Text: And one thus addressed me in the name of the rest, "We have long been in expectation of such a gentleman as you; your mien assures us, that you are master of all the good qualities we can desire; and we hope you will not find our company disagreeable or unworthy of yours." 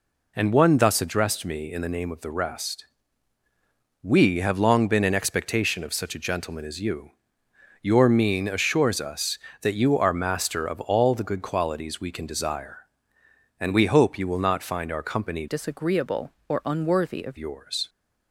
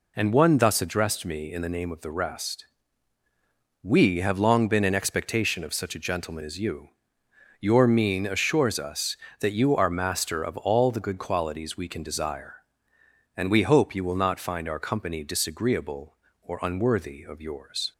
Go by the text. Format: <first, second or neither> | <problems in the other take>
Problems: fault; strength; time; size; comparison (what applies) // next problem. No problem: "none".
second | changes voice from "disagreeable" to "of"; from 15.4 to 17.3 s; 1.9 s long